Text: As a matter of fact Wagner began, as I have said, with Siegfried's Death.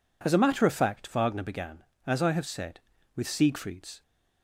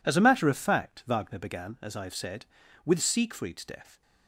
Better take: second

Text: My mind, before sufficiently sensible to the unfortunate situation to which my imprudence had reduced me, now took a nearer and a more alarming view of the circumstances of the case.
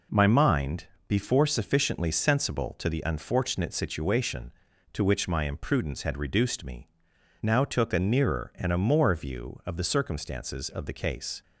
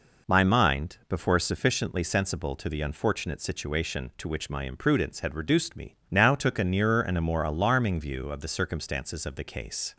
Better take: second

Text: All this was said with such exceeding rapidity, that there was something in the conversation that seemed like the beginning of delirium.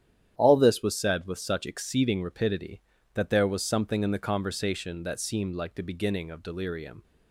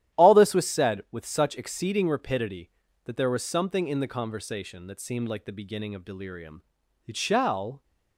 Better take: first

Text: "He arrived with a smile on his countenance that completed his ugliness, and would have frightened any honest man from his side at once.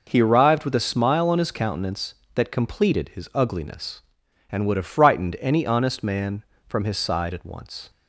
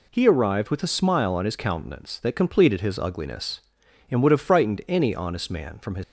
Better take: first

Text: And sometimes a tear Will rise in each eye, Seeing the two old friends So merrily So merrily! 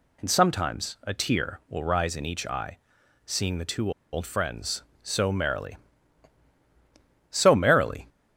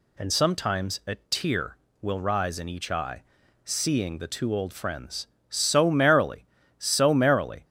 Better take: second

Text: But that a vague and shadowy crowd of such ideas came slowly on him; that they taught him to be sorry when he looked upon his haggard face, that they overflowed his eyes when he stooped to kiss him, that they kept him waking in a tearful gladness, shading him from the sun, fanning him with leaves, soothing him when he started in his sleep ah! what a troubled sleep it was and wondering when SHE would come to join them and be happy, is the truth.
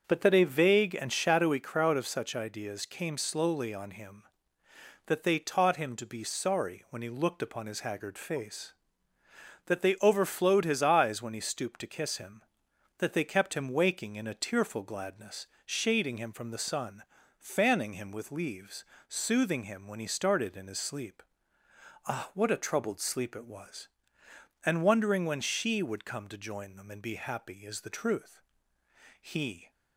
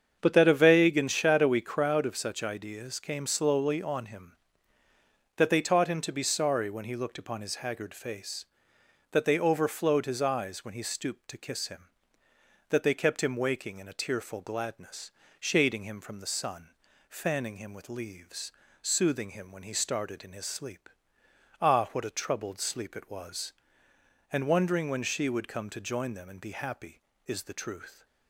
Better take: second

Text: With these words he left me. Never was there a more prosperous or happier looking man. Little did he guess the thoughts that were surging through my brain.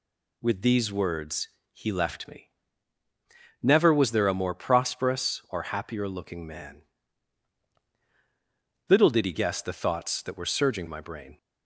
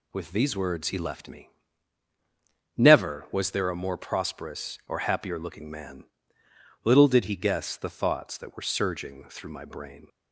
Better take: second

